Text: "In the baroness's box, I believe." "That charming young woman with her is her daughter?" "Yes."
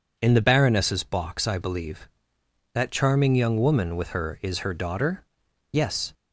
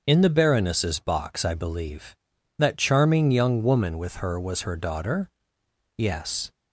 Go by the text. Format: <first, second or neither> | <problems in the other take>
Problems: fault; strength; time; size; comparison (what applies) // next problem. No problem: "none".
first | starts louder than the rest; until 1.0 s; 6.5 dB // says "was" for "is"; at 4.4 s